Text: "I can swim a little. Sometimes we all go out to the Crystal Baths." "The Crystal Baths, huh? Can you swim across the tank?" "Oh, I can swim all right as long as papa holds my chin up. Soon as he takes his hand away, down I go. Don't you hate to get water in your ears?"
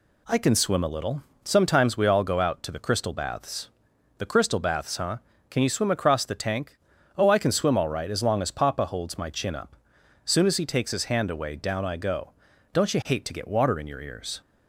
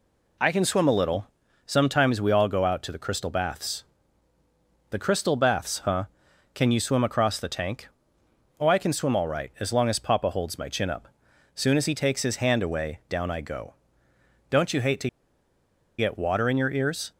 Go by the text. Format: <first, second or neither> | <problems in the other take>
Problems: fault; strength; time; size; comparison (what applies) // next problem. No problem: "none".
first | pauses between "to" and "get"; noticeable; at 15.0 s; 0.90 s long